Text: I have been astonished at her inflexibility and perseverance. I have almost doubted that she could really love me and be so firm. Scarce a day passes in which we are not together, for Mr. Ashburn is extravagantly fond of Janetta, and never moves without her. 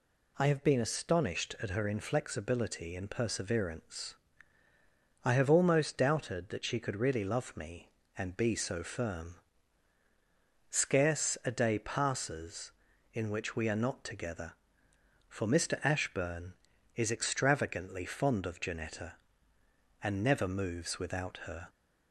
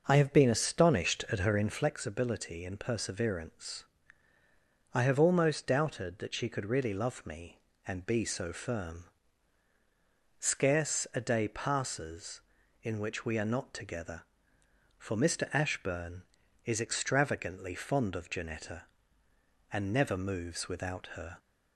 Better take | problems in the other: first | starts louder than the rest; noticeable; until 1.9 s; 6 dB

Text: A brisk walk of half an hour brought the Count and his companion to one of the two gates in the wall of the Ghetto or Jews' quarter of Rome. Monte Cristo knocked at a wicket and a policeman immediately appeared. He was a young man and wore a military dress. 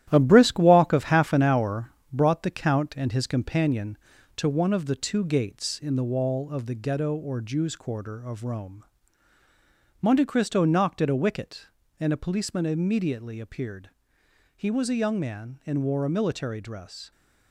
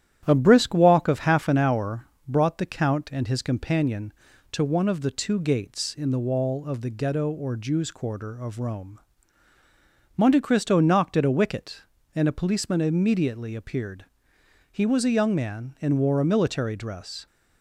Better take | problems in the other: second | gets quieter; strong; throughout; 7.5 dB // starts louder than the rest; strong; until 1.1 s; 12.5 dB; strong in the second // pauses between "hour" and "brought"; slight; at 1.9 s; 0.20 s long; slight in the second

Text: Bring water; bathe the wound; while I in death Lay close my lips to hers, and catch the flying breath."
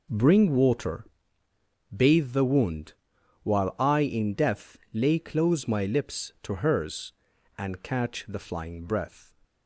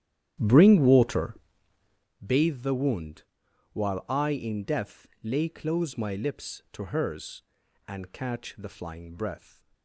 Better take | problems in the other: first | starts louder than the rest; strong; until 2.2 s; 11.5 dB

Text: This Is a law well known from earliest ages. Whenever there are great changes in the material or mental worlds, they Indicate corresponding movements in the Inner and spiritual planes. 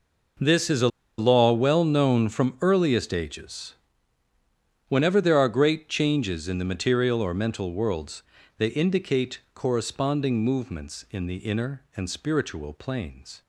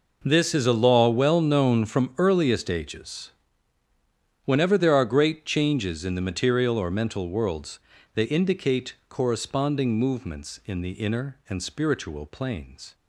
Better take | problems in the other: second | pauses between "a" and "law"; slight; at 0.8 s; 0.30 s long

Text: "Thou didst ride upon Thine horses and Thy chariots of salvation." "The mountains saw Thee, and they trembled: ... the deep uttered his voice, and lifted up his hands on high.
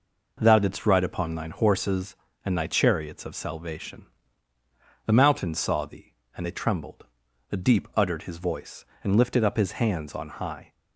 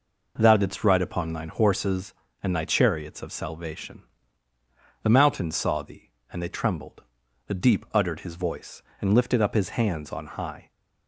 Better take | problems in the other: neither | none

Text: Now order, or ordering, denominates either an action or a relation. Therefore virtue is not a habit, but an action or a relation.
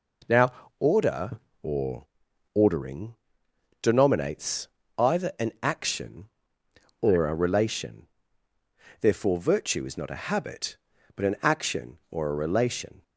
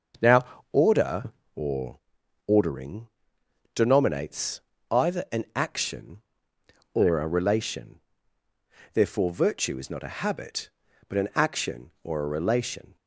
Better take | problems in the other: first | starts louder than the rest; until 1.3 s; 6.5 dB // pauses between "Now" and "order"; slight; at 0.4 s; 0.28 s long; slight in the first // pauses between "or" and "ordering"; noticeable; at 1.9 s; 0.48 s long; noticeable in the first // pauses between "denominates" and "either"; slight; at 4.5 s; 0.32 s long; slight in the first

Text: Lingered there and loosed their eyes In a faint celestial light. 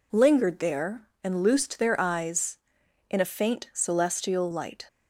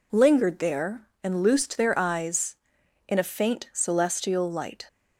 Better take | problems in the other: neither | none

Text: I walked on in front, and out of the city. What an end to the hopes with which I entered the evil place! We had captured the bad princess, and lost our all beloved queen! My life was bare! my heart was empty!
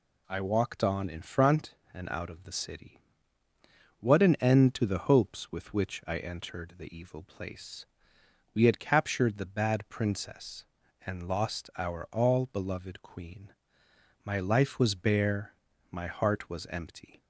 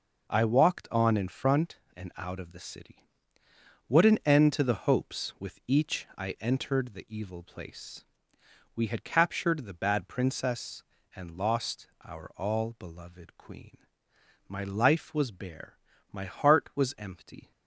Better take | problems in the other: first | says "each" for "which"; at 5.6 s

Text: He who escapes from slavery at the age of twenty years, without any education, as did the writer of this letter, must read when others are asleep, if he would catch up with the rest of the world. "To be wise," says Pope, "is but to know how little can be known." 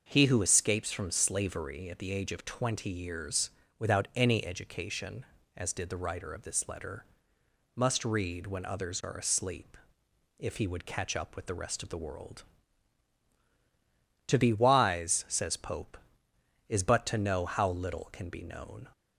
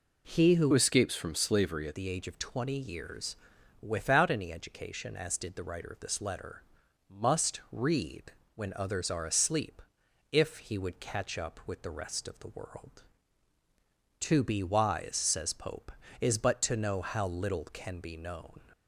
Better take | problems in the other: first | changes voice from "escapes" to "at"; from 0.7 to 1.9 s; 1.2 s long // pauses between "read" and "when"; slight; at 8.3 s; 0.24 s long

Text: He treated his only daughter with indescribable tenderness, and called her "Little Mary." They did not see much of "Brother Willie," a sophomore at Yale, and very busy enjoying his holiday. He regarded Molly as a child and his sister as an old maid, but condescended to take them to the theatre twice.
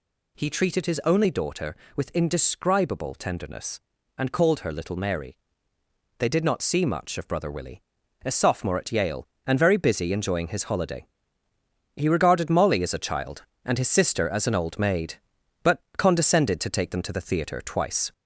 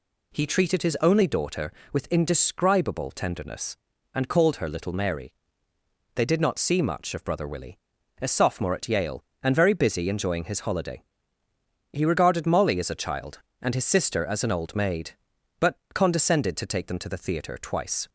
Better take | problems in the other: second | gets louder; slight; throughout; 2.5 dB

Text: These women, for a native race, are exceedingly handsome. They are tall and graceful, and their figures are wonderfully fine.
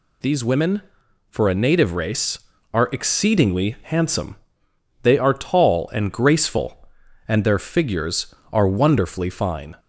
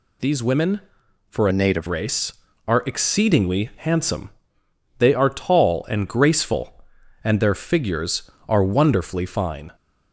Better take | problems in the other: first | changes voice from "a" to "native"; from 1.5 to 1.8 s; 0.3 s long

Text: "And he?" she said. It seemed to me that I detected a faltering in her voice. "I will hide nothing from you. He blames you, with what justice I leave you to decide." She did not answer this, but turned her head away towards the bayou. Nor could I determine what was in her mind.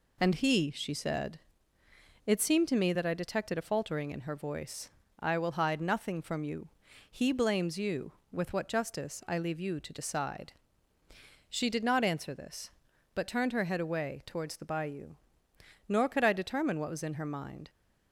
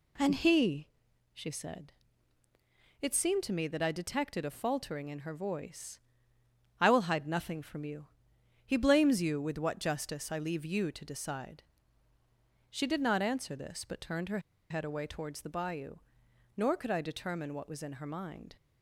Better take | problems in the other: first | pauses between "her" and "head"; slight; at 14.4 s; 0.29 s long

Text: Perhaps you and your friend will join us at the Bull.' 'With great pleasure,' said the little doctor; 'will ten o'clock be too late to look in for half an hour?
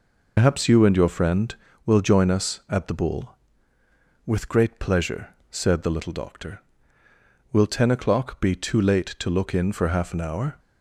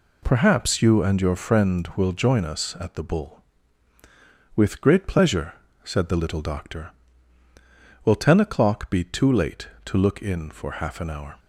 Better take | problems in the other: second | loses the start of "Perhaps"; at 0.3 s; 80 ms

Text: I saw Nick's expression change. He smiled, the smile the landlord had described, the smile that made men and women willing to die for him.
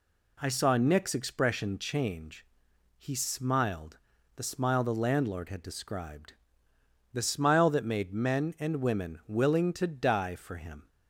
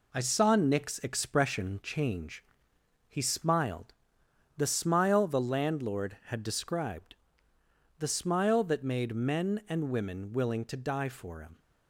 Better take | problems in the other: first | gets quieter; noticeable; throughout; 5 dB

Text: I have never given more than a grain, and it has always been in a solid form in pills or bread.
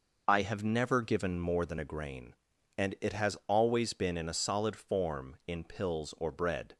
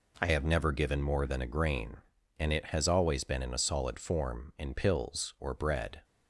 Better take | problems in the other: first | changes voice at "have"; from 0.3 s on; 5.7 s long

